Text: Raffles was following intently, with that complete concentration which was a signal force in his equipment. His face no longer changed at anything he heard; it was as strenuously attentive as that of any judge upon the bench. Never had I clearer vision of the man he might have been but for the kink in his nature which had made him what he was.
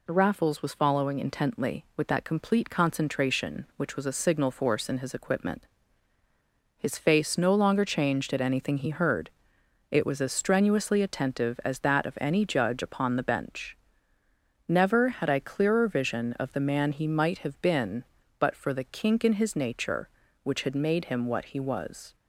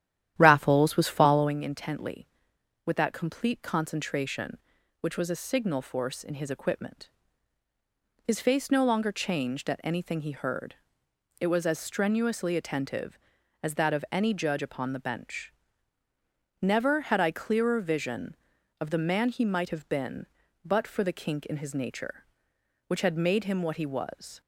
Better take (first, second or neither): first